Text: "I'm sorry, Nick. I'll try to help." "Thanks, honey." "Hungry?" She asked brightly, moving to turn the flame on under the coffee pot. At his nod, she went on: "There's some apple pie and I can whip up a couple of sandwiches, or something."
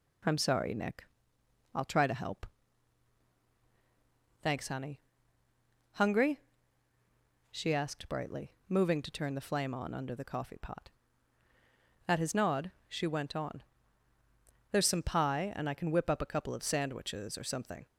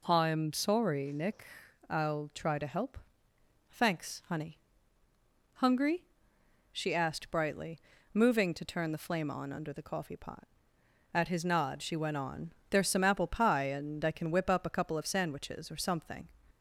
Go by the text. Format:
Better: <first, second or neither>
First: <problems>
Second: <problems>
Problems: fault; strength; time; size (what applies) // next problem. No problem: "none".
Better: second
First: skips "apple"; at 15.0 s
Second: none